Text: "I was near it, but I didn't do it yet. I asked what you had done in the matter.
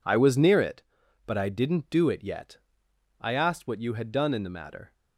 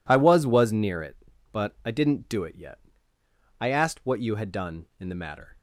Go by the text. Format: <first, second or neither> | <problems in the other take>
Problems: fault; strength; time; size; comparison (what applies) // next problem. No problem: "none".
first | says "was" twice; at 0.4 s